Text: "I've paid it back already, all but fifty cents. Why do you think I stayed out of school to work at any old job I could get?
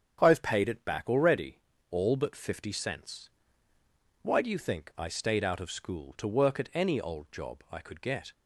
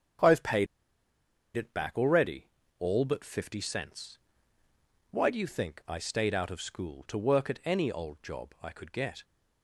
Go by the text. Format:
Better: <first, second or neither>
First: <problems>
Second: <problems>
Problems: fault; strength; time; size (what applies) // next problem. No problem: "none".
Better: first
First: starts louder than the rest; strong; until 1.2 s; 7.5 dB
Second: starts louder than the rest; strong; until 2.1 s; 7.5 dB // pauses between "paid" and "it"; noticeable; at 0.6 s; 0.89 s long